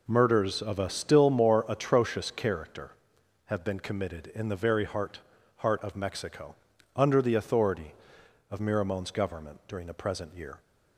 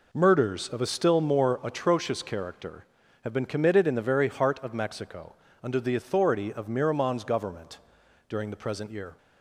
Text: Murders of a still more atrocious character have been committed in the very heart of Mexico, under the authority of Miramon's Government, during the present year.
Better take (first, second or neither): second